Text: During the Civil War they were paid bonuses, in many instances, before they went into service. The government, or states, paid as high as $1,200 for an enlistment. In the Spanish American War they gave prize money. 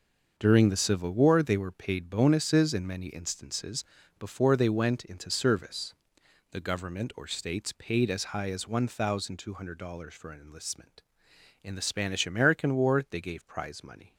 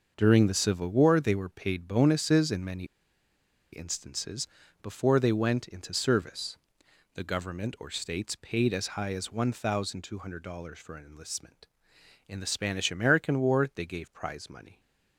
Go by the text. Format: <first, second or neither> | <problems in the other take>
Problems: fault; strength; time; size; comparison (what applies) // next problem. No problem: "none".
first | starts louder than the rest; until 1.1 s; 6.5 dB; also in the first // pauses between "many" and "instances"; noticeable; at 2.8 s; 0.88 s long